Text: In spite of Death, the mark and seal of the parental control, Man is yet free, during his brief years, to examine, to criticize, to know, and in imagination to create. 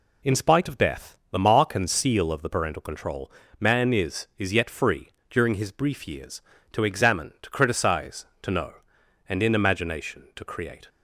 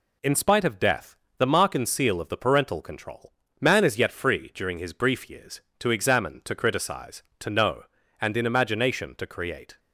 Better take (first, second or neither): second